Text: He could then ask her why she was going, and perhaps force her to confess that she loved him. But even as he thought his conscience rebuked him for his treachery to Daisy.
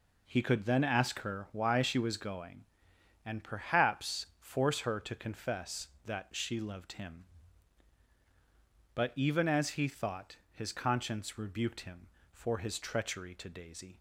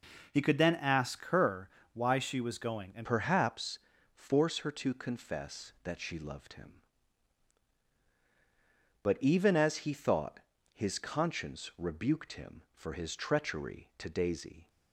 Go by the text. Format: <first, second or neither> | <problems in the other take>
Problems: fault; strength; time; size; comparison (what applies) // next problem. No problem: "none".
first | pauses between "her" and "why"; slight; at 1.6 s; 0.26 s long // changes voice at "perhaps"; from 3.0 s on; 11.6 s long // pauses between "perhaps" and "force"; slight; at 3.7 s; 0.34 s long // pauses between "thought" and "his"; slight; at 10.3 s; 0.34 s long; slight in the first